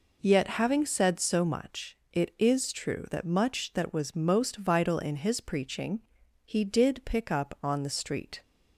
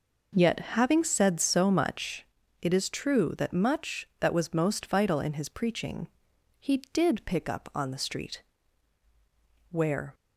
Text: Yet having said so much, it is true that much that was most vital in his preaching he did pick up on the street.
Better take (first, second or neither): first